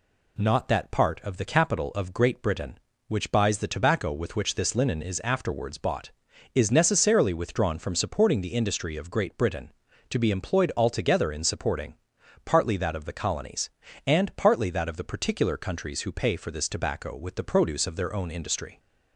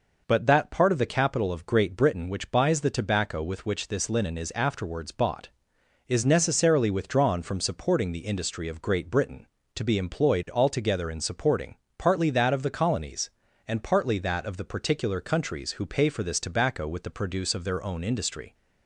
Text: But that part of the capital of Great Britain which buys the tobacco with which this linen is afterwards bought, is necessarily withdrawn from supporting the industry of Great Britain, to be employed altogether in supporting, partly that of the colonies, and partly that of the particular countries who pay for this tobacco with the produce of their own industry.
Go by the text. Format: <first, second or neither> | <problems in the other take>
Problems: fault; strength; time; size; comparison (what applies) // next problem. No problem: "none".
second | says "Not" for "But"; at 0.3 s